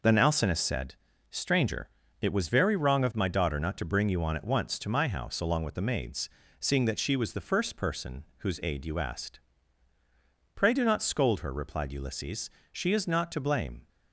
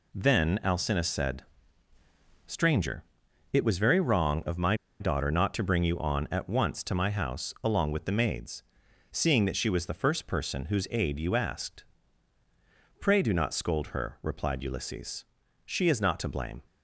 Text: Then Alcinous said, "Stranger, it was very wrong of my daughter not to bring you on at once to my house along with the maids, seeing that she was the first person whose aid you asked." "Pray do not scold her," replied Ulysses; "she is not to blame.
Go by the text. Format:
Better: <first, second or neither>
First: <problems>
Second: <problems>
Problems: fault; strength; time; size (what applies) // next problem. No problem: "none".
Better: first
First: none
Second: pauses between "my" and "daughter"; slight; at 4.7 s; 0.25 s long